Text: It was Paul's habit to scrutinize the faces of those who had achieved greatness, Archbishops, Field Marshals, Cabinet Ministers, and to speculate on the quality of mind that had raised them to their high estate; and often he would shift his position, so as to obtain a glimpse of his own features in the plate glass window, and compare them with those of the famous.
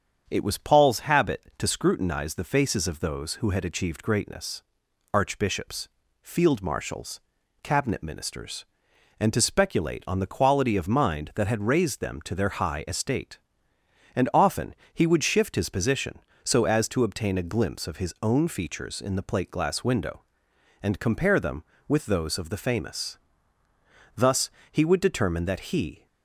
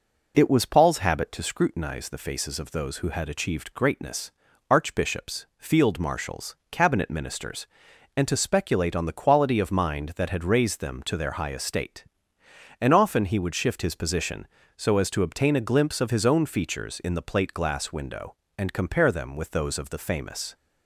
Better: second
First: starts louder than the rest; strong; until 1.2 s; 7.5 dB // pauses between "often" and "he"; slight; at 14.7 s; 0.18 s long // goes on to say "Thus he would determine that he"; strong; from 24.1 s on; 1.9 s long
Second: none

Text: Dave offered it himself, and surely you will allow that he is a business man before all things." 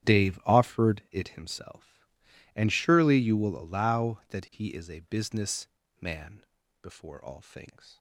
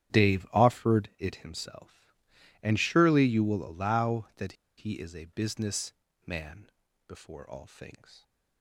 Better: first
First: starts louder than the rest; strong; until 1.2 s; 10 dB // pauses between "business" and "man"; slight; at 5.6 s; 0.32 s long // pauses between "man" and "before"; at 6.4 s; 0.38 s long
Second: starts louder than the rest; strong; until 1.2 s; 10 dB // pauses between "that" and "he"; slight; at 4.5 s; 0.24 s long // pauses between "business" and "man"; slight; at 5.9 s; 0.32 s long // pauses between "man" and "before"; at 6.6 s; 0.38 s long

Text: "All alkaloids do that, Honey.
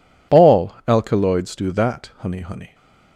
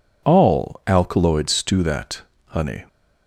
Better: second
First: says "Honey" twice; at 2.4 s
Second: none

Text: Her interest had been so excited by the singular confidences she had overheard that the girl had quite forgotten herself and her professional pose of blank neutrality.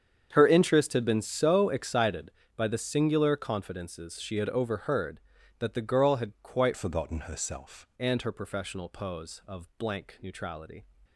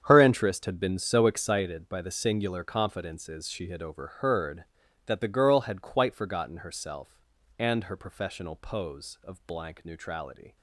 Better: second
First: starts louder than the rest; strong; until 1.3 s; 7.5 dB // changes voice from "forgotten" to "herself"; from 6.7 to 7.8 s; 1.1 s long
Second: starts louder than the rest; strong; until 1.0 s; 8 dB

